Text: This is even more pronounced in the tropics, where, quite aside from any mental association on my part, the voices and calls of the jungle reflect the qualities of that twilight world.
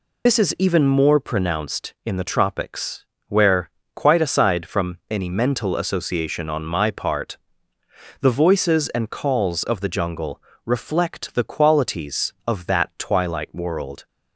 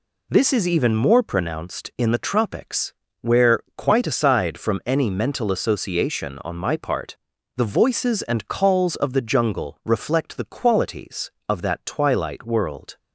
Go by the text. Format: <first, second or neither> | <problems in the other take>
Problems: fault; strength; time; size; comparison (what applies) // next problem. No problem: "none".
second | loses the start of "This"; at 0.2 s; 60 ms // pauses between "jungle" and "reflect"; slight; at 10.4 s; 0.24 s long